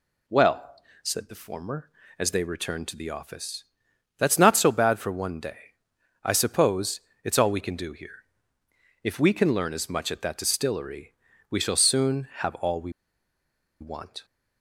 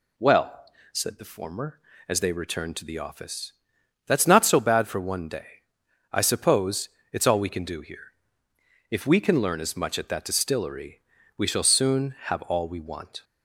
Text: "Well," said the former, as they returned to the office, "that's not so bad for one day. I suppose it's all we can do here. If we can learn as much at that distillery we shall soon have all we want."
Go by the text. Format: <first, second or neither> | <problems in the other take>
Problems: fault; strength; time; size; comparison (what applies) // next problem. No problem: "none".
second | pauses between "suppose" and "it's"; slight; at 6.9 s; 0.24 s long; slight in the second // pauses between "distillery" and "we"; slight; at 11.1 s; 0.36 s long; slight in the second // pauses between "we" and "want"; noticeable; at 12.9 s; 0.90 s long